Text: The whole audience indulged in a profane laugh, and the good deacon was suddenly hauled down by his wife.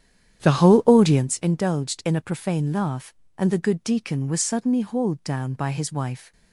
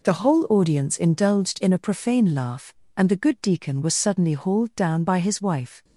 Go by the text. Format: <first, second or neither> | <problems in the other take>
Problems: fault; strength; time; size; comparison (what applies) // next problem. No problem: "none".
second | starts louder than the rest; strong; until 1.3 s; 10 dB